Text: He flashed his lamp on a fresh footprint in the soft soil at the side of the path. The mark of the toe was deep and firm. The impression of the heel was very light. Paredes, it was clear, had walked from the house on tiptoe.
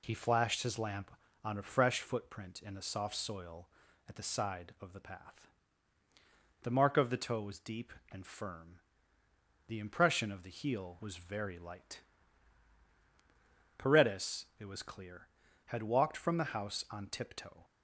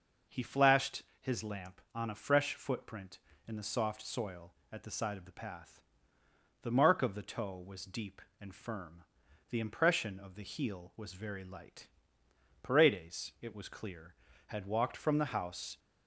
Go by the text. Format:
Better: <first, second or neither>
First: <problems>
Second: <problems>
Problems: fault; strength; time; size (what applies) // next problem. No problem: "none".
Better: first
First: none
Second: pauses between "flashed" and "his"; slight; at 1.0 s; 0.16 s long // stops before "on tiptoe"; at 15.7 s